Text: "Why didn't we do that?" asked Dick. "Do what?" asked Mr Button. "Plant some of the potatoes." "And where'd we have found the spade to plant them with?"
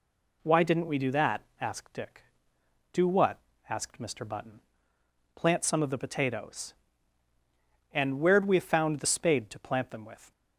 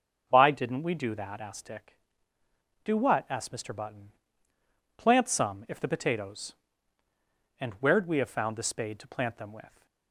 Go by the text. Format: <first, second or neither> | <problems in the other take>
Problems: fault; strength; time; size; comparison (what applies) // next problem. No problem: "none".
first | says "if" for "of"; at 5.6 s